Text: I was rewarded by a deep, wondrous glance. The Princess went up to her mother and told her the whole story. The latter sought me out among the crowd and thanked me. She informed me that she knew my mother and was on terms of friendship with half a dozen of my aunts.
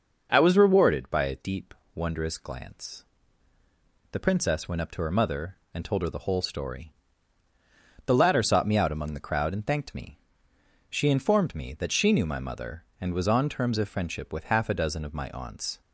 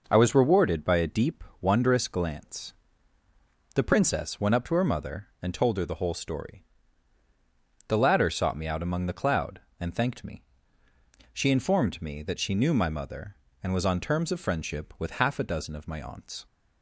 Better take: first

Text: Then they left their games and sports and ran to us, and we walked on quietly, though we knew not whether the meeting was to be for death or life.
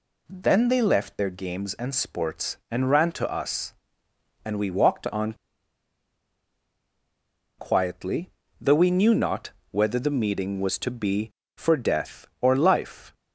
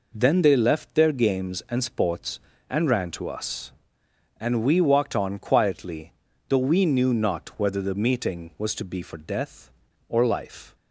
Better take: second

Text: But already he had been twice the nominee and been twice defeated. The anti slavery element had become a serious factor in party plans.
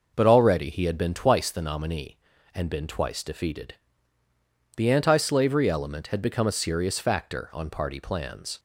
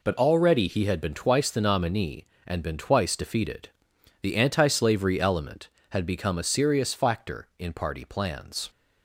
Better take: second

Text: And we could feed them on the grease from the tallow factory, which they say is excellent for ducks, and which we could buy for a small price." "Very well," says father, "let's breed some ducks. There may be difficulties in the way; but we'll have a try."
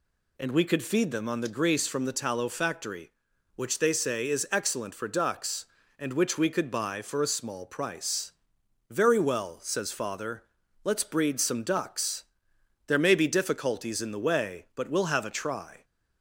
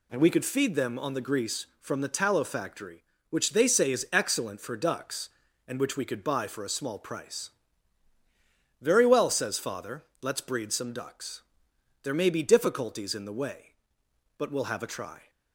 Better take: neither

